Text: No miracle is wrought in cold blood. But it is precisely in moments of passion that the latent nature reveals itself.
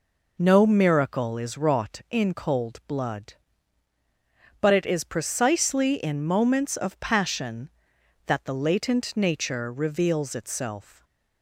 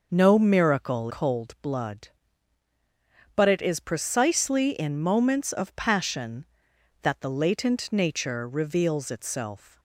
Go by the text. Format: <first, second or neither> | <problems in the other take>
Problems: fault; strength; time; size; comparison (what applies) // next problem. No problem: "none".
first | skips "is wrought in"; at 1.0 s